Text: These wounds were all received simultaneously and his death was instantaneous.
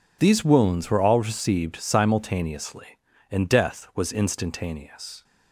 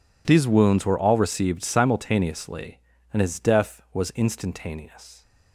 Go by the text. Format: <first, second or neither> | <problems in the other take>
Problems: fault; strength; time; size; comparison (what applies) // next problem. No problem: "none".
second | skips "his"; at 3.4 s